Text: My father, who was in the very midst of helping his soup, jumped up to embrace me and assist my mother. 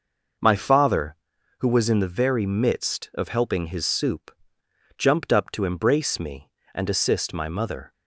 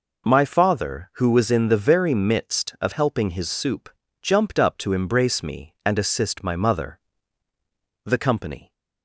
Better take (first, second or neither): first